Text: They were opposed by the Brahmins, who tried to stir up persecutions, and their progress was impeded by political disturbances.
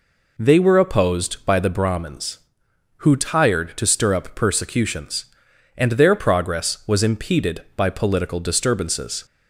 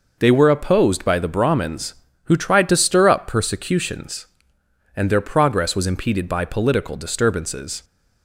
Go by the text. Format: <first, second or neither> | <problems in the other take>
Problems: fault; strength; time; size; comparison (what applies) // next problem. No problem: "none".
second | says "tired" for "tried"; at 3.1 s